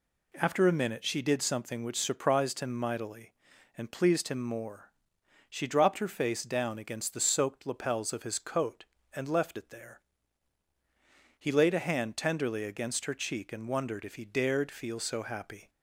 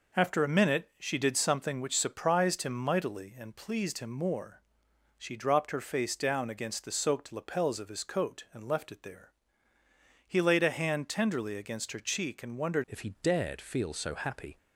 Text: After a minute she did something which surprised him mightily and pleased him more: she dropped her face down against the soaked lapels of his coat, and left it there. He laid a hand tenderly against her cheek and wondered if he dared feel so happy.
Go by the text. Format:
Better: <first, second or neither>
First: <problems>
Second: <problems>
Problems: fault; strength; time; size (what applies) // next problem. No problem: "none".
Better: first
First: none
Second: changes voice at "if"; from 12.8 s on; 1.7 s long